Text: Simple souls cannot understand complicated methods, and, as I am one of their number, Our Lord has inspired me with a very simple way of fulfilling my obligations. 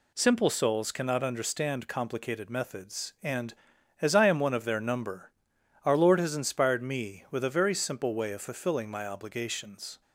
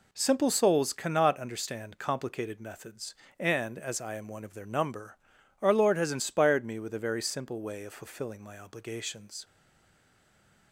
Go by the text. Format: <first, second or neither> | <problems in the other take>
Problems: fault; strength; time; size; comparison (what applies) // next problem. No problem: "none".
first | stays silent after the last word; noticeable; from 9.4 s on; 1.3 s long